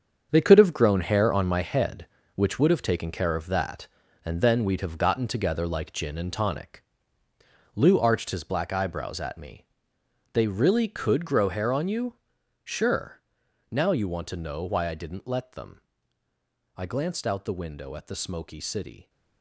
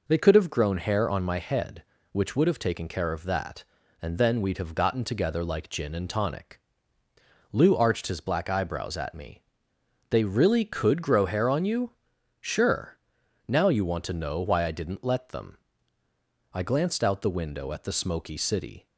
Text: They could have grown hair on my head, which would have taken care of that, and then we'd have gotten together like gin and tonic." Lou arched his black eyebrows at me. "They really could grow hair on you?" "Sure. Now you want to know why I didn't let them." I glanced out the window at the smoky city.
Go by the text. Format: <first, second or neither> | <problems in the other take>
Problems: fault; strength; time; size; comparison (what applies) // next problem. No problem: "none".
second | gets quieter; strong; throughout; 10.5 dB